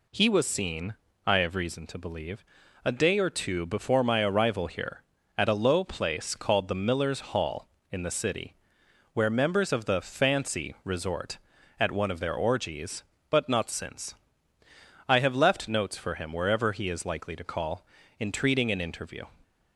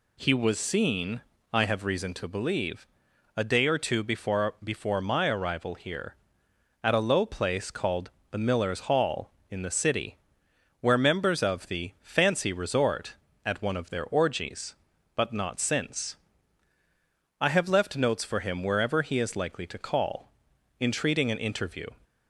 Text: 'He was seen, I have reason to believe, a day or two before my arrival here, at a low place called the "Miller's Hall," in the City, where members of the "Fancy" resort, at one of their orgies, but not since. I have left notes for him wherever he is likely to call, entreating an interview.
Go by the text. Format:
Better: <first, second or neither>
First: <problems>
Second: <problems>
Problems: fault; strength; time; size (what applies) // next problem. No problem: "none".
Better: first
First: none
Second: says "before" twice; at 4.6 s // pauses between "called" and "the"; slight; at 8.1 s; 0.22 s long